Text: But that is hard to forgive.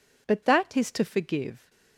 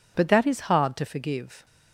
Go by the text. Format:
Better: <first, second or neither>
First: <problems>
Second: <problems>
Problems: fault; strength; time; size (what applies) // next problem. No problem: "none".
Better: second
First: skips "hard"; at 0.9 s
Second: none